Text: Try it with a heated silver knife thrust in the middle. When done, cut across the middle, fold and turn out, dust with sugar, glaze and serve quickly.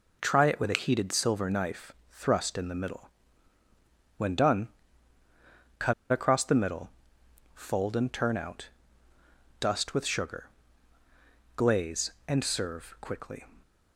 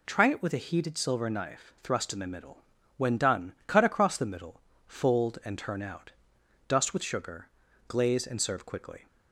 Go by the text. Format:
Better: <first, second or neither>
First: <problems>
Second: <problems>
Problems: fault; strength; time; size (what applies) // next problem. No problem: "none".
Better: second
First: pauses between "knife" and "thrust"; slight; at 1.9 s; 0.20 s long // pauses between "cut" and "across"; slight; at 5.9 s; 0.19 s long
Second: none